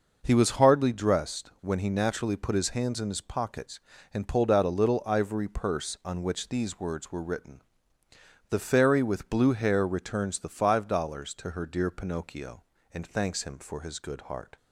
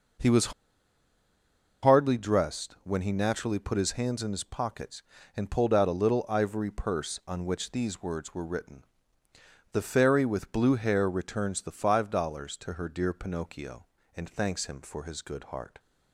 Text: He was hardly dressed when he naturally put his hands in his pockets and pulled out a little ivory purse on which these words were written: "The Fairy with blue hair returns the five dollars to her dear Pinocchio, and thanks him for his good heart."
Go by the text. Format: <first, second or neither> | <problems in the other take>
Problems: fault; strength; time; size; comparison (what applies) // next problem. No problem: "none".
first | pauses between "was" and "hardly"; strong; at 0.5 s; 1.3 s long